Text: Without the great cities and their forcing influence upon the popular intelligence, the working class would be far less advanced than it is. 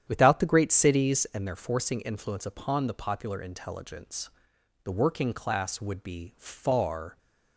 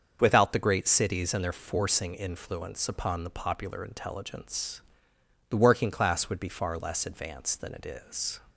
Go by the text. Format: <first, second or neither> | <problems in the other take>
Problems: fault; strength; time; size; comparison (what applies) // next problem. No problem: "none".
second | starts louder than the rest; strong; until 1.0 s; 9.5 dB; also in the second // stops before "less advanced than it is"; at 7.1 s